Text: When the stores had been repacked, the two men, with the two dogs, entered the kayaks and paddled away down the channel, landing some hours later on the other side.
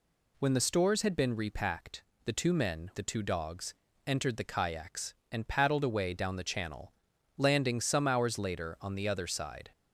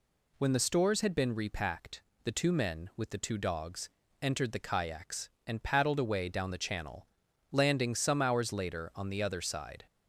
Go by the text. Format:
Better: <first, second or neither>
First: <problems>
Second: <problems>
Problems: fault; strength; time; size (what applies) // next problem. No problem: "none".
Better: second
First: skips "with"; at 2.9 s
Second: none